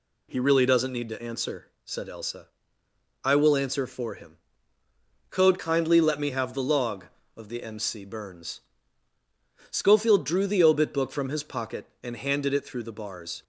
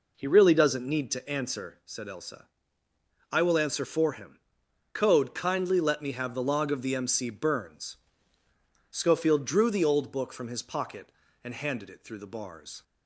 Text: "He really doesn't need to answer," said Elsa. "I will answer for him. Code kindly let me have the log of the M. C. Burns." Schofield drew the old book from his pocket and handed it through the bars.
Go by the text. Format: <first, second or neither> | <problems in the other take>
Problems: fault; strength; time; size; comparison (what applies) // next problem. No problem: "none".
second | says "obit" for "old"; at 10.6 s